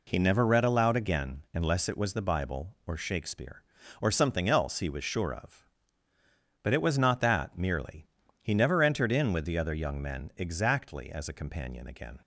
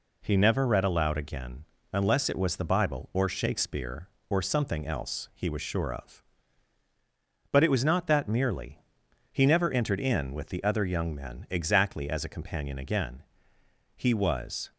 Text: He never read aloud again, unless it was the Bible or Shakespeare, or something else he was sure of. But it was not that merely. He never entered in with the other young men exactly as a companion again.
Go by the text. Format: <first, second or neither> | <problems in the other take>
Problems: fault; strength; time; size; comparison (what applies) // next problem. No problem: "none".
first | goes on to say "He was"; noticeable; from 13.9 s on; 0.76 s long